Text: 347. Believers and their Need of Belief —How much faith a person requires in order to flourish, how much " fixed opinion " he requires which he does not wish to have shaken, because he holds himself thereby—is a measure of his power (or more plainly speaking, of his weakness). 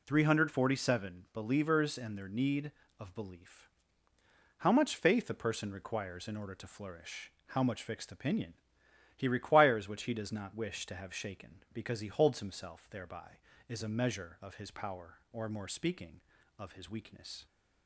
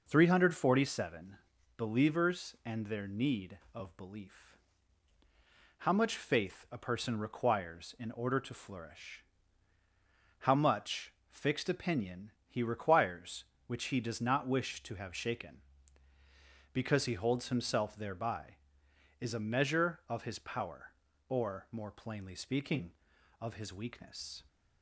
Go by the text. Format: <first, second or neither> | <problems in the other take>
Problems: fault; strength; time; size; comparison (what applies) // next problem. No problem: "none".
second | skips "plainly"; at 15.6 s